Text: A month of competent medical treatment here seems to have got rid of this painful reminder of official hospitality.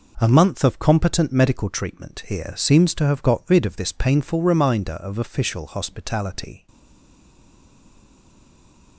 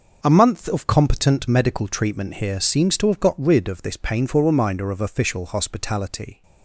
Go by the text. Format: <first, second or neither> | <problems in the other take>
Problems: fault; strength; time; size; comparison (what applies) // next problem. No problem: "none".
second | stays silent after the last word; from 6.6 s on; 2.3 s long